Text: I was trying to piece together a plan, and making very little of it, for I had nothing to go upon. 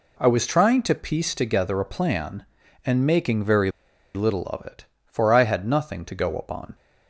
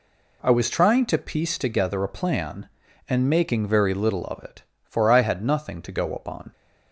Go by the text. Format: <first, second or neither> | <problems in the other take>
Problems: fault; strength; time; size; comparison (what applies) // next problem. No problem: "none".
second | pauses between "very" and "little"; at 3.6 s; 0.45 s long